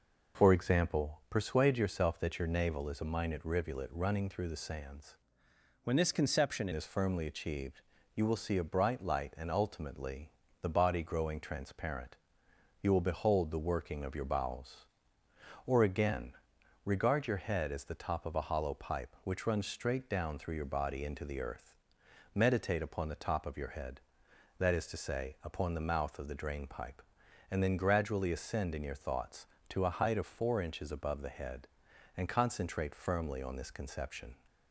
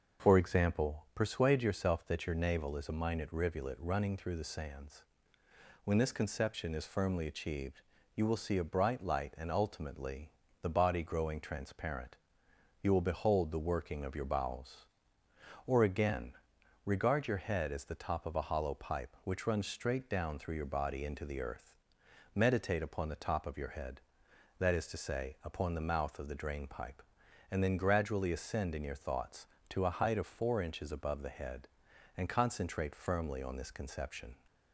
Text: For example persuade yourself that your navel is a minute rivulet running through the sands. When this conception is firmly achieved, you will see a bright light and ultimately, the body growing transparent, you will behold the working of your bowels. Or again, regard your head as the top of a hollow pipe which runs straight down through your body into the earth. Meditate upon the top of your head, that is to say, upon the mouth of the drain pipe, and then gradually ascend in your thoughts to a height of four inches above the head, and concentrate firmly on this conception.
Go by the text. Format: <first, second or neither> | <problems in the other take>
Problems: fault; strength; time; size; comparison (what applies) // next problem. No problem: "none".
second | changes voice from "When" to "conception"; from 5.8 to 6.6 s; 0.8 s long